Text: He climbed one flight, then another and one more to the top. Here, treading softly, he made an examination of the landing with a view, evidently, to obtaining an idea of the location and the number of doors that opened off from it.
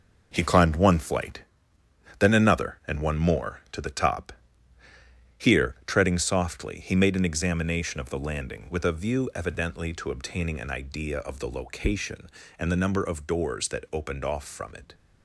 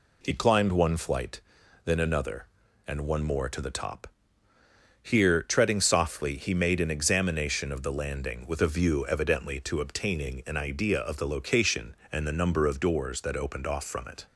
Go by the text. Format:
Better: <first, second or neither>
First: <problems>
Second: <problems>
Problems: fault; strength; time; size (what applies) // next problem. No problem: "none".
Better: second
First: gets quieter; strong; throughout; 8.5 dB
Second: none